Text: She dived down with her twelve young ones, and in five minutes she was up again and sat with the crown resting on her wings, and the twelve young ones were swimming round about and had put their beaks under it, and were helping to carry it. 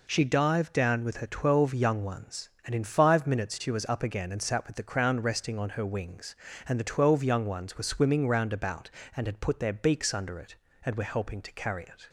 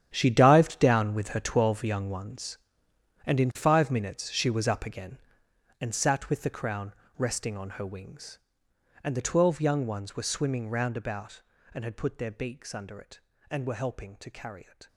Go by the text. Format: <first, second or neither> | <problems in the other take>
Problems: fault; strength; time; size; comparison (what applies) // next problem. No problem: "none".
first | gets quieter; strong; throughout; 14.5 dB // pauses between "crown" and "resting"; slight; at 6.9 s; 0.24 s long